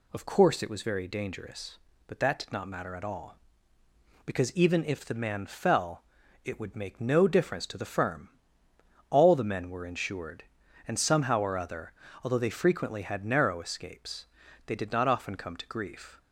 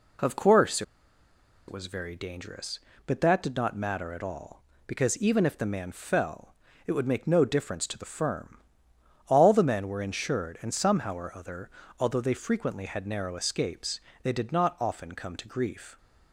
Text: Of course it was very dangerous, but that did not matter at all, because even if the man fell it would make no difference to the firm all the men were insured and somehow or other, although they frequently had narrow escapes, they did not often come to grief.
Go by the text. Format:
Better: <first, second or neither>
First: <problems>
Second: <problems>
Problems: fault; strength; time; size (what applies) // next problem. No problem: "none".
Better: first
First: pauses between "fell" and "it"; at 6.0 s; 0.42 s long // pauses between "firm" and "all"; noticeable; at 8.2 s; 0.80 s long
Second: pauses between "course" and "it"; noticeable; at 0.8 s; 0.85 s long // pauses between "fell" and "it"; slight; at 6.5 s; 0.34 s long // pauses between "firm" and "all"; noticeable; at 8.5 s; 0.72 s long